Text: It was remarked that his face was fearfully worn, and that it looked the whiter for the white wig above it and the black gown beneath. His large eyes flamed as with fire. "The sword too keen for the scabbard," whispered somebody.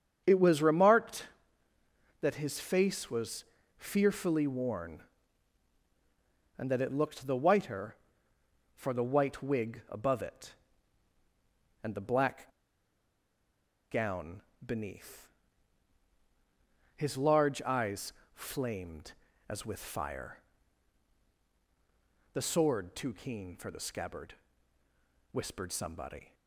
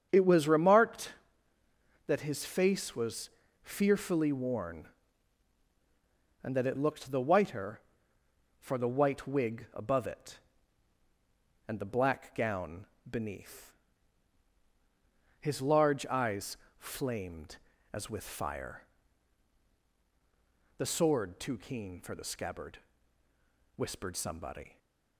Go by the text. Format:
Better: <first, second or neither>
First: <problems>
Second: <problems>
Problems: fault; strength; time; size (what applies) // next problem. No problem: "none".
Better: second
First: starts louder than the rest; strong; until 1.2 s; 8 dB // pauses between "was" and "fearfully"; slight; at 3.4 s; 0.32 s long // pauses between "black" and "gown"; strong; at 12.4 s; 1.4 s long // pauses between "gown" and "beneath"; slight; at 14.4 s; 0.24 s long // pauses between "eyes" and "flamed"; slight; at 18.1 s; 0.22 s long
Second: starts louder than the rest; strong; until 1.1 s; 8 dB // pauses between "was" and "fearfully"; slight; at 3.2 s; 0.32 s long // pauses between "gown" and "beneath"; slight; at 12.8 s; 0.24 s long // pauses between "eyes" and "flamed"; slight; at 16.5 s; 0.22 s long